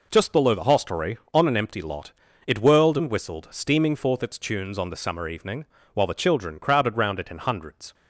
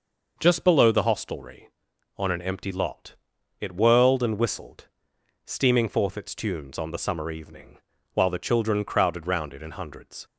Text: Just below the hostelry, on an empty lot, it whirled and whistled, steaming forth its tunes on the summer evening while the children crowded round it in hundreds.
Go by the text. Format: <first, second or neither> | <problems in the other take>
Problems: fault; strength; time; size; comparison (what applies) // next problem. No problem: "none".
neither | pauses between "evening" and "while"; the same in both